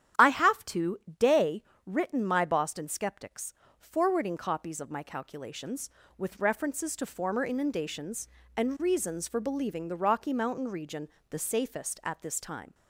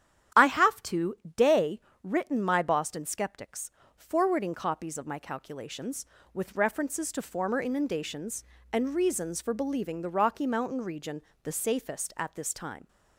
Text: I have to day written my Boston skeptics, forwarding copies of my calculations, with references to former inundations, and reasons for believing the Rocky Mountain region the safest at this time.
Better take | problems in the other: neither | starts louder than the rest; strong; the same in both // pauses between "to" and "day"; slight; the same in both // pauses between "day" and "written"; slight; the same in both // pauses between "region" and "the"; slight; the same in both

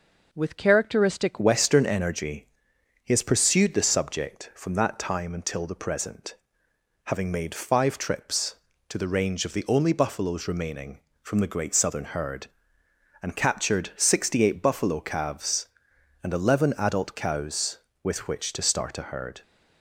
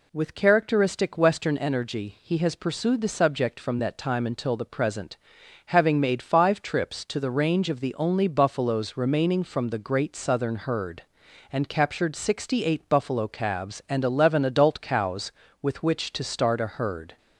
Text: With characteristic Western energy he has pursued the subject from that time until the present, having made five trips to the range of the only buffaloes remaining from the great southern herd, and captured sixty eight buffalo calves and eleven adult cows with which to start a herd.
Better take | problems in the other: second | changes voice at "Western"; from 1.3 s on; 18.1 s long // pauses between "energy" and "he"; noticeable; at 2.4 s; 0.56 s long

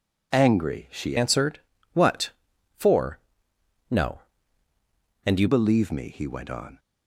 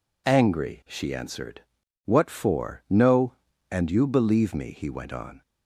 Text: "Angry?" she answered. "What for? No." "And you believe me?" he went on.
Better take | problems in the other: second | changes voice from "answered" to "you"; from 1.1 to 5.4 s; 4.3 s long

